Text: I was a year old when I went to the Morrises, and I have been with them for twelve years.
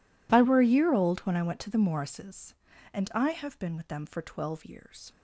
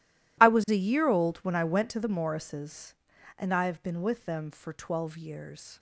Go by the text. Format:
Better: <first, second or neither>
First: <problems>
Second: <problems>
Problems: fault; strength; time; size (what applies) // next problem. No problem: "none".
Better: second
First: says "were" for "was"; at 0.4 s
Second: none